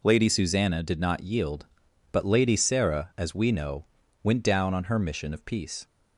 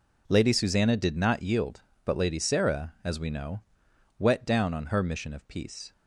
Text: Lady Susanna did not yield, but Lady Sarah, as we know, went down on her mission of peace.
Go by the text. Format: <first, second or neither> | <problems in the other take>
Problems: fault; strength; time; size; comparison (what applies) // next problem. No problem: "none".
first | says "wet" for "went"; at 4.1 s